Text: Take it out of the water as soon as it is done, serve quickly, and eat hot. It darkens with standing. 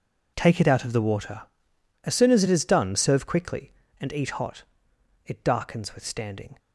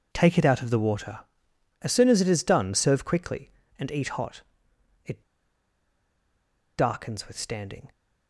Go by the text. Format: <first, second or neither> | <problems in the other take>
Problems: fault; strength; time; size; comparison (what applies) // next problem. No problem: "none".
first | pauses between "It" and "darkens"; strong; at 5.2 s; 1.5 s long